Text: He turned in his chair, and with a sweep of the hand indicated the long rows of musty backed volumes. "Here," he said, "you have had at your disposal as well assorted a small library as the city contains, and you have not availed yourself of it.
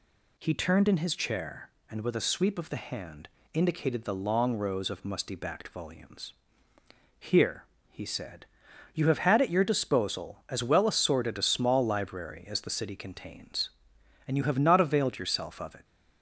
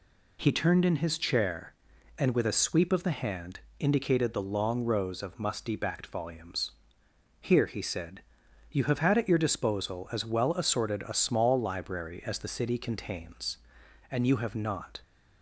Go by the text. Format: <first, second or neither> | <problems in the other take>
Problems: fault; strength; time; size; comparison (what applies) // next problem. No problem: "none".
first | pauses between "hand" and "indicated"; slight; at 3.6 s; 0.18 s long; slight in the first // stops before "availed yourself of it"; at 15.0 s